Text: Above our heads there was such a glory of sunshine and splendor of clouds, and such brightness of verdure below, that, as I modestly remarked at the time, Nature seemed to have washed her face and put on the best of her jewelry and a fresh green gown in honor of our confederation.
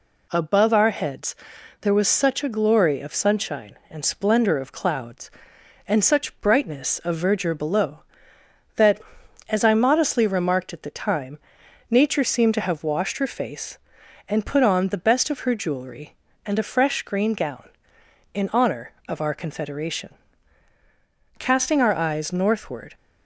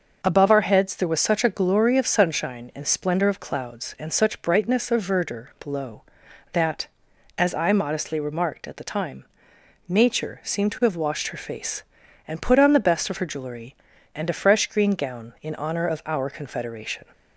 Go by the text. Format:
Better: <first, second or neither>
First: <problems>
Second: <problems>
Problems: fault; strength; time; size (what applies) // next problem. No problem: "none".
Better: second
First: pauses between "heads" and "there"; noticeable; at 1.3 s; 0.46 s long // goes on to say "Casting our eyes northward"; from 21.3 s on; 1.5 s long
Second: none